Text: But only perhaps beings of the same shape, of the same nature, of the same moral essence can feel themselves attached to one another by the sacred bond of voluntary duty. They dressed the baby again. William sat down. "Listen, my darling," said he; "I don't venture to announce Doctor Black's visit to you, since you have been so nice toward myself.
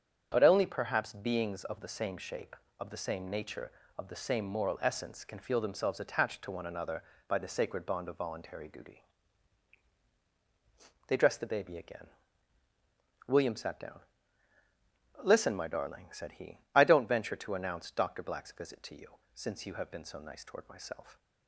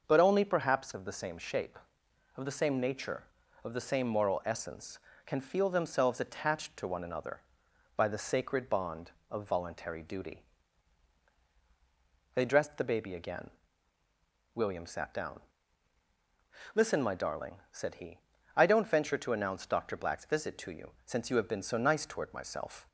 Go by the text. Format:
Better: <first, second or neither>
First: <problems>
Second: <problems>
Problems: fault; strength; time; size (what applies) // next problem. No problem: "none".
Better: first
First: starts louder than the rest; strong; until 1.3 s; 8 dB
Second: starts louder than the rest; until 1.0 s; 6.5 dB // skips "beings"; at 0.9 s